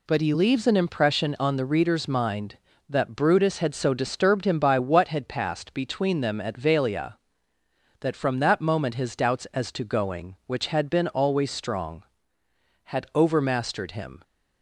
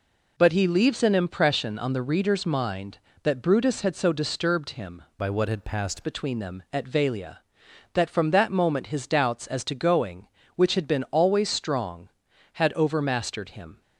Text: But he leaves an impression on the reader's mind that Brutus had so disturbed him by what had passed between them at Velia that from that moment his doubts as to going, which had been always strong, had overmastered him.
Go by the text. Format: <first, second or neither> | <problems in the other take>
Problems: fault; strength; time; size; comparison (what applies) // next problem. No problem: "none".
first | changes voice from "by" to "passed"; from 5.1 to 6.0 s; 0.9 s long